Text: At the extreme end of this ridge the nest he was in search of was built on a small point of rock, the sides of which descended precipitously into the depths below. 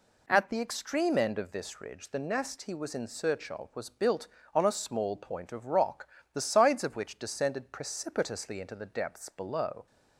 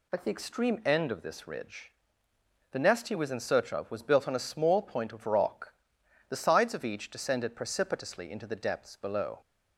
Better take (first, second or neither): first